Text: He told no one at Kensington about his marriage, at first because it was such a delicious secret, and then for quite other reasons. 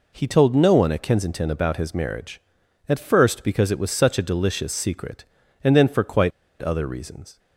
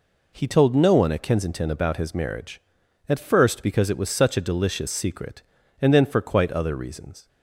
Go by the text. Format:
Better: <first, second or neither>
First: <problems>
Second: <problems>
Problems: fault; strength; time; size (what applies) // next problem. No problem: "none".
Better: second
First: pauses between "quite" and "other"; slight; at 6.3 s; 0.31 s long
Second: none